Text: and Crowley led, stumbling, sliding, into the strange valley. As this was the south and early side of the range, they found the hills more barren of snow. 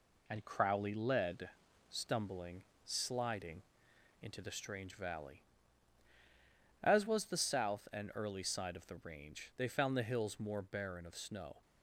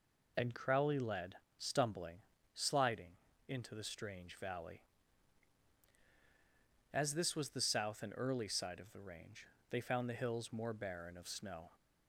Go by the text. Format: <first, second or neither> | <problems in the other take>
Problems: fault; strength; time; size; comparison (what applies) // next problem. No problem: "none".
second | skips "this"; at 7.0 s